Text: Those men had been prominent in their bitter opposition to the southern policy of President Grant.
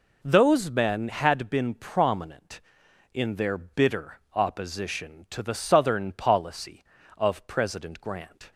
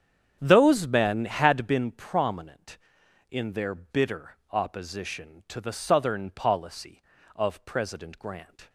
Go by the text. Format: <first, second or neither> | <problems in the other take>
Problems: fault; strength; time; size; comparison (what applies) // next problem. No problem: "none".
first | starts louder than the rest; strong; until 1.9 s; 8 dB